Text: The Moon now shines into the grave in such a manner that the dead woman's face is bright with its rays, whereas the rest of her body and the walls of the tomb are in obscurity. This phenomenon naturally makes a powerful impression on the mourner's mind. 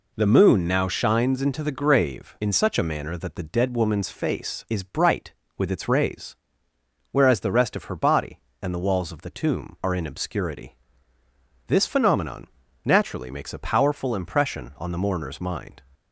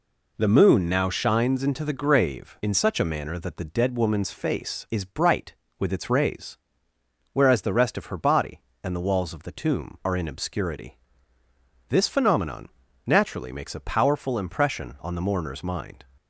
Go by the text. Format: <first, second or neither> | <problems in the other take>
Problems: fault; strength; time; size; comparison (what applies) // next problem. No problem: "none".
neither | pauses between "phenomenon" and "naturally"; the same in both